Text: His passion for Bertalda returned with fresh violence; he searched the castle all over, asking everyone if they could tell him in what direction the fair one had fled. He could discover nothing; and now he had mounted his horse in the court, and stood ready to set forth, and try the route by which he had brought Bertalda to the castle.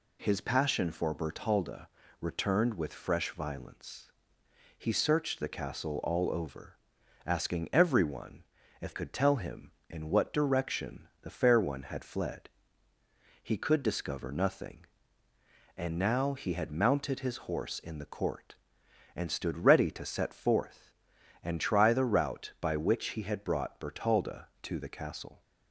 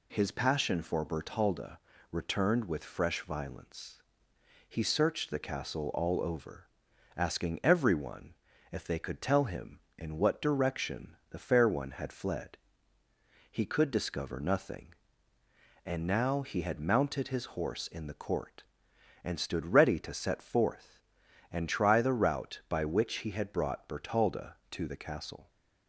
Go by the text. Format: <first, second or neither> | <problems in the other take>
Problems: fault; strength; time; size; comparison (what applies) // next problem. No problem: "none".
second | pauses between "Bertalda" and "returned"; slight; at 1.8 s; 0.32 s long; slight in the second // pauses between "everyone" and "if"; at 8.4 s; 0.38 s long; also in the second // skips "they"; at 8.9 s